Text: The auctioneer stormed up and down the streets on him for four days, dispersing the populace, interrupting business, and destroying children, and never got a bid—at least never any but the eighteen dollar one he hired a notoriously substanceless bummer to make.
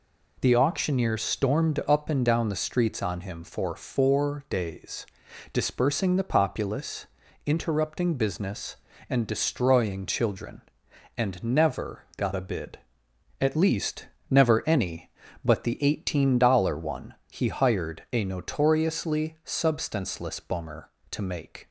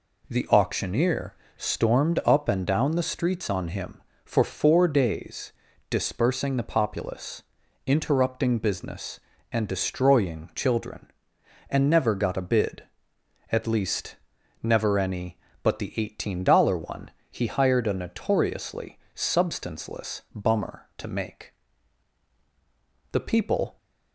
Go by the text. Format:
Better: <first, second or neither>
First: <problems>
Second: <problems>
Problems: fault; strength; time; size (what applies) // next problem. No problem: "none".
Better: first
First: pauses between "least" and "never"; slight; at 14.0 s; 0.24 s long // pauses between "one" and "he"; slight; at 17.1 s; 0.18 s long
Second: pauses between "auctioneer" and "stormed"; slight; at 1.3 s; 0.20 s long // pauses between "least" and "never"; noticeable; at 14.1 s; 0.48 s long // pauses between "one" and "he"; slight; at 17.1 s; 0.18 s long // pauses between "notoriously" and "substanceless"; slight; at 18.9 s; 0.16 s long // goes on to say "The people"; noticeable; from 23.1 s on; 0.66 s long